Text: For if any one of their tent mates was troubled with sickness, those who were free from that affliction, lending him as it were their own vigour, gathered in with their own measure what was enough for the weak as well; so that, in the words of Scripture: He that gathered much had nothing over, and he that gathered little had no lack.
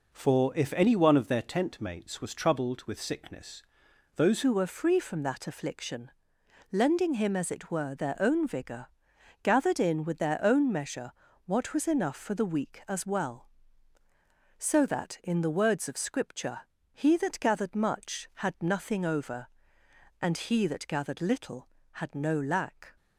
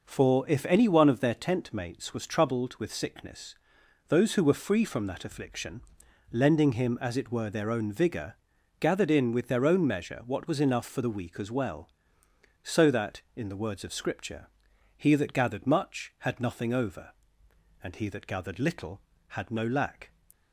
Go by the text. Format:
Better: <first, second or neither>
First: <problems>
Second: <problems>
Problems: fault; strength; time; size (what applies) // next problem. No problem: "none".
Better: second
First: changes voice at "who"; from 4.4 s on; 18.5 s long // pauses between "measure" and "what"; slight; at 11.1 s; 0.34 s long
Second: none